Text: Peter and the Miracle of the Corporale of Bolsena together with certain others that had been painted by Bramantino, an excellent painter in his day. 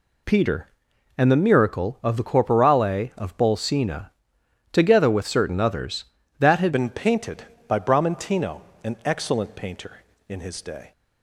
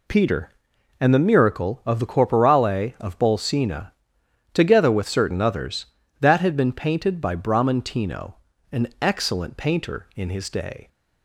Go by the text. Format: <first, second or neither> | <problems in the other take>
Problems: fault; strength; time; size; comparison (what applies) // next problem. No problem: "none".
second | pauses between "Bolsena" and "together"; noticeable; at 4.1 s; 0.62 s long; noticeable in the second // changes voice at "been"; from 6.7 s on; 4.2 s long